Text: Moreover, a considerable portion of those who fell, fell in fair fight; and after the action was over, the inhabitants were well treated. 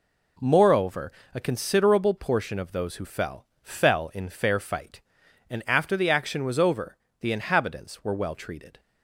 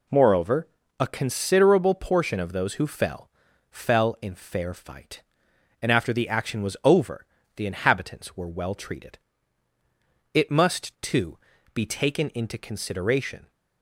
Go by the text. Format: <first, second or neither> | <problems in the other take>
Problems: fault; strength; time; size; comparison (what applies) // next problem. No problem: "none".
first | goes on to say "It must too be taken into consideration"; strong; from 10.3 s on; 3.1 s long